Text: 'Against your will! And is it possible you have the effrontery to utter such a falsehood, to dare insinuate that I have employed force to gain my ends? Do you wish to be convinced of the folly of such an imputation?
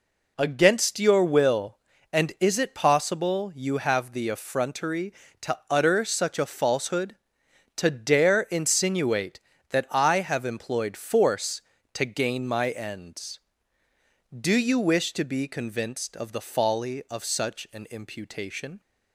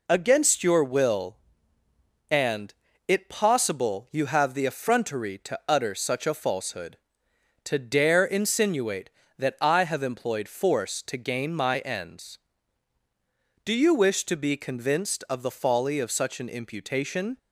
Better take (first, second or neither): first